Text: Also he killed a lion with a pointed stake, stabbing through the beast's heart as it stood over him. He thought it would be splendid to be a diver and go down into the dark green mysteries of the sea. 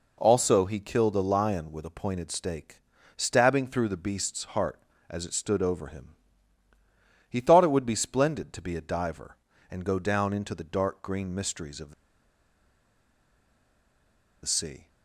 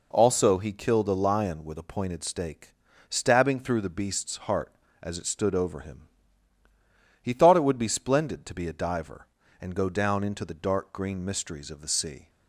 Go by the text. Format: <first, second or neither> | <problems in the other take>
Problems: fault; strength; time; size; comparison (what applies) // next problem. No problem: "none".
second | pauses between "the" and "sea"; strong; at 11.9 s; 2.5 s long